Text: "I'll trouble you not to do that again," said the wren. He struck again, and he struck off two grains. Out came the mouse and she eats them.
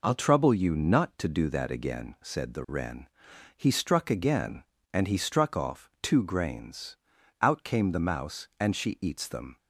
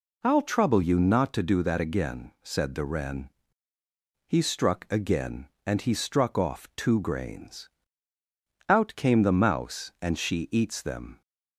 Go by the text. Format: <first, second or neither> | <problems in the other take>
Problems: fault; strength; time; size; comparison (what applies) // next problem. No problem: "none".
neither | none